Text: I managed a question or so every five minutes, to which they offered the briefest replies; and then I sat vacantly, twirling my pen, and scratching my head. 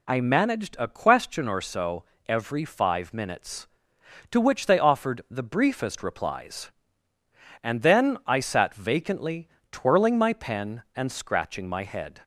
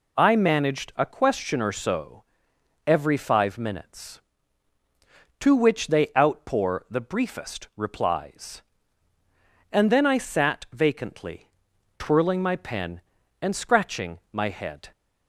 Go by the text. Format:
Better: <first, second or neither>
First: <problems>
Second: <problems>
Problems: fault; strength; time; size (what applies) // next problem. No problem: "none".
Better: first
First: pauses between "so" and "every"; slight; at 2.0 s; 0.24 s long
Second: pauses between "so" and "every"; noticeable; at 2.2 s; 0.64 s long // says "outpour" for "offered"; at 6.1 s